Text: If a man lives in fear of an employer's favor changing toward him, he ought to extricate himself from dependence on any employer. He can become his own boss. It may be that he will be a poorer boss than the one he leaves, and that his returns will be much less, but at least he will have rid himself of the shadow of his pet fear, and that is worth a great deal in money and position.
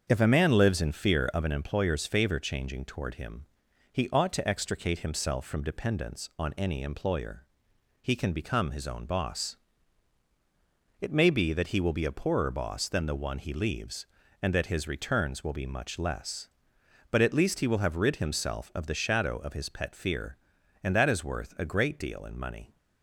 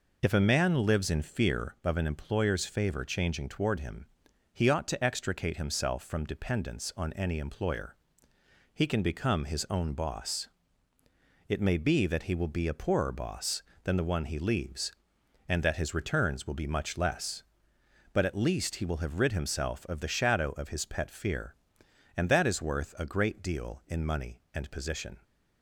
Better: second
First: starts louder than the rest; until 1.1 s; 7 dB // stops before "and position"; at 22.7 s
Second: none

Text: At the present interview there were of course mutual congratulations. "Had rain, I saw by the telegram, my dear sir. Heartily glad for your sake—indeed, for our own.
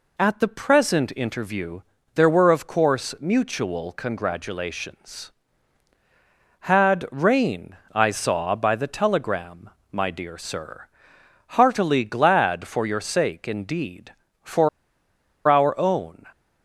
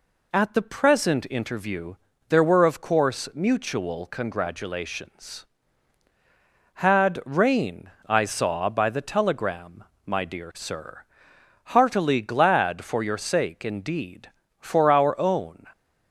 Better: second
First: pauses between "interview" and "there"; slight; at 1.7 s; 0.34 s long // pauses between "for" and "our"; noticeable; at 14.6 s; 0.78 s long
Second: pauses between "interview" and "there"; slight; at 1.9 s; 0.34 s long

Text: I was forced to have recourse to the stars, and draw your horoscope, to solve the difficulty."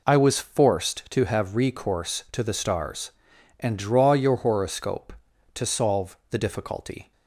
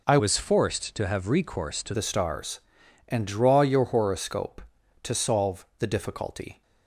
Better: first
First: none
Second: changes voice from "was" to "to"; from 0.1 to 1.9 s; 1.8 s long

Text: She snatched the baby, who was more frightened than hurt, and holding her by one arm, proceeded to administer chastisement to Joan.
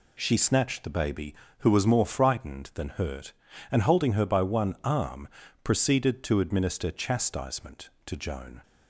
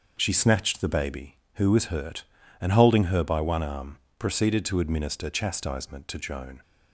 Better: first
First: none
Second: starts louder than the rest; until 1.1 s; 6.5 dB // skips "more frightened than"; at 1.8 s

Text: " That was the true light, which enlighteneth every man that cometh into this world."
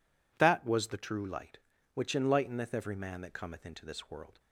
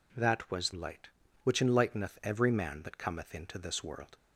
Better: first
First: none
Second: skips "the true"; at 0.7 s

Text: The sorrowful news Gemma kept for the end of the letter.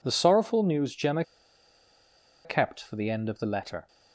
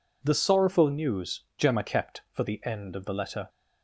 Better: second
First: pauses between "Gemma" and "kept"; at 1.2 s; 1.2 s long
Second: none

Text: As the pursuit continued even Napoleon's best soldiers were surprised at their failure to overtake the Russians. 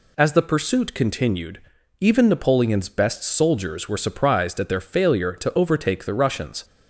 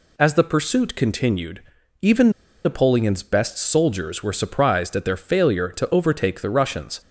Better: first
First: pauses between "continued" and "even"; at 1.6 s; 0.40 s long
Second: pauses between "continued" and "even"; at 1.6 s; 0.40 s long // pauses between "even" and "Napoleon's"; slight; at 2.2 s; 0.34 s long

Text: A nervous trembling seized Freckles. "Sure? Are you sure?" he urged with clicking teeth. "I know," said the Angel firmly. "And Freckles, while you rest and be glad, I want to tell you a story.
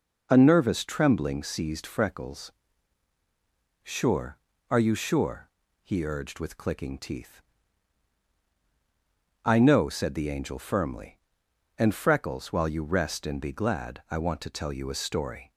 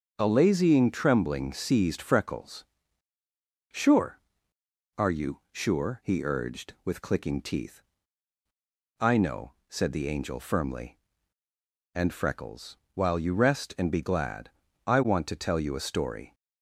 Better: first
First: none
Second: starts louder than the rest; until 1.1 s; 7 dB // says "lazying" for "nervous"; at 0.2 s

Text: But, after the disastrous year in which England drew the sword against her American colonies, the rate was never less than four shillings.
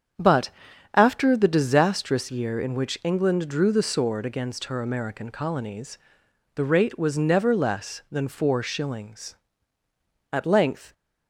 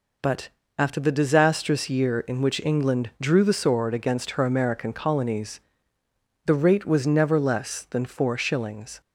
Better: second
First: starts louder than the rest; strong; until 1.6 s; 8 dB // goes on to say "At length"; noticeable; from 10.3 s on; 0.62 s long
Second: none

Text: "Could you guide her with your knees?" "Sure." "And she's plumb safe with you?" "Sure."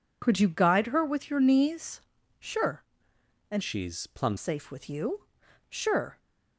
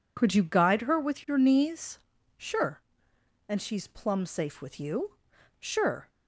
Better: second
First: changes voice from "she's" to "plumb"; from 3.6 to 4.3 s; 0.7 s long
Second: none

